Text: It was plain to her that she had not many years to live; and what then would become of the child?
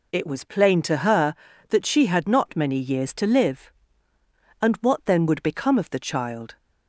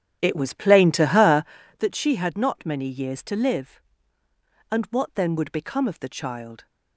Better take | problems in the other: first | starts louder than the rest; strong; until 1.8 s; 10.5 dB

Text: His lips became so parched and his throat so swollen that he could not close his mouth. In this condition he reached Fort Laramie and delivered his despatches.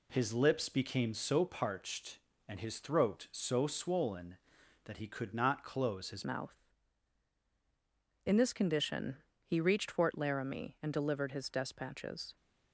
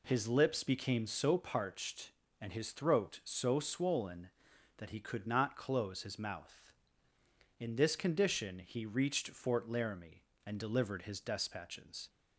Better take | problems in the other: second | changes voice at "mouth"; from 6.2 s on; 6.1 s long // pauses between "condition" and "he"; slight; at 9.1 s; 0.26 s long

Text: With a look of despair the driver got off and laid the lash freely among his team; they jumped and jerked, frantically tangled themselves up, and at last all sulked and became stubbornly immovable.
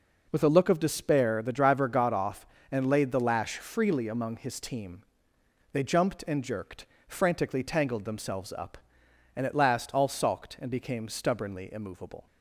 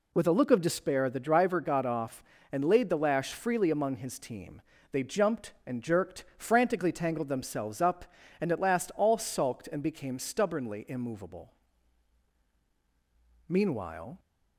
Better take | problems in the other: first | goes on to say "Meanwhile"; noticeable; from 13.4 s on; 0.70 s long

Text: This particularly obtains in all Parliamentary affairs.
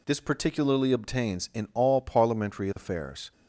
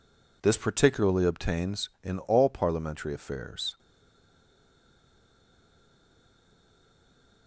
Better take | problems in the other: first | stays silent after the last word; strong; from 3.7 s on; 3.7 s long

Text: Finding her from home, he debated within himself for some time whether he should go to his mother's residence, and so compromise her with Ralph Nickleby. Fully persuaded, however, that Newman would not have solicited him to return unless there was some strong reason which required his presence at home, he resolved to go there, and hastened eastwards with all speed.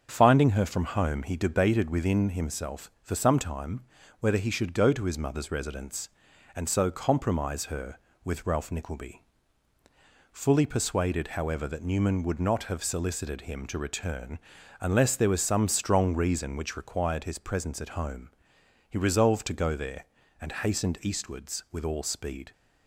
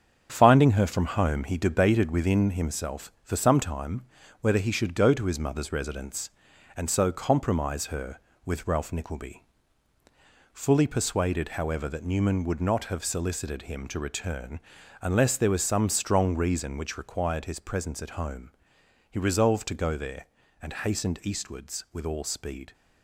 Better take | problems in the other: first | gets quieter; noticeable; throughout; 5.5 dB // starts louder than the rest; strong; until 1.3 s; 7.5 dB; also in the first // pauses between "time" and "whether"; slight; at 4.0 s; 0.34 s long; slight in the first // pauses between "return" and "unless"; at 14.6 s; 0.40 s long; also in the first

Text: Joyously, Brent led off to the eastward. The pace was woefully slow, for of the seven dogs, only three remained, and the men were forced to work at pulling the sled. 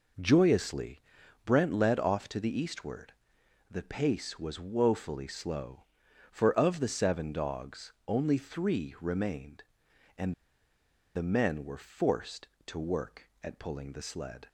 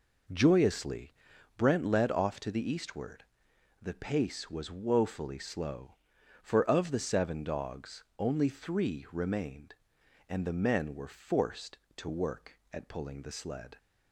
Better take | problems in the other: second | pauses between "and" and "the"; noticeable; at 10.3 s; 0.82 s long

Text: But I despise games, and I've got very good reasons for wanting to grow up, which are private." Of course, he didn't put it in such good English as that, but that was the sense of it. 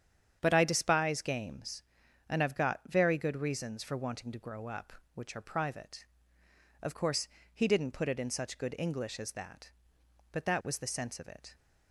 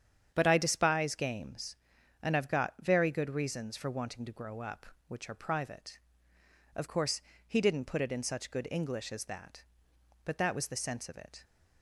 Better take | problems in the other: neither | starts louder than the rest; strong; the same in both

